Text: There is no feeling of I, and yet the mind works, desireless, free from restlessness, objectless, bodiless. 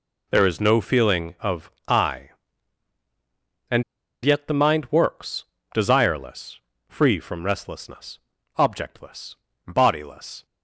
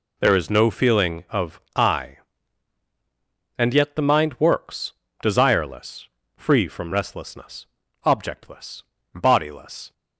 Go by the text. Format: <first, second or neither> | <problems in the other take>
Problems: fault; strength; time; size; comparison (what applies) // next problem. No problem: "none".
second | pauses between "of" and "I"; slight; at 1.6 s; 0.18 s long; slight in the second // pauses between "and" and "yet"; at 3.8 s; 0.41 s long